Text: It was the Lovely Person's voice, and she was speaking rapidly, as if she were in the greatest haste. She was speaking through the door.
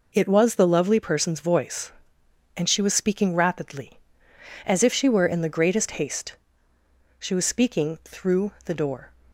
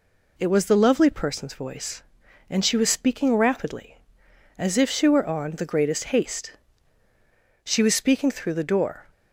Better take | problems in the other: first | says "on" for "in"; at 5.2 s

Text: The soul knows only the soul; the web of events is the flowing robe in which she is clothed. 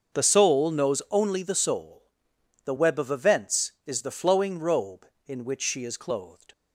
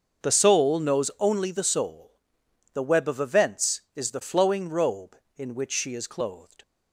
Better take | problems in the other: neither | starts louder than the rest; the same in both

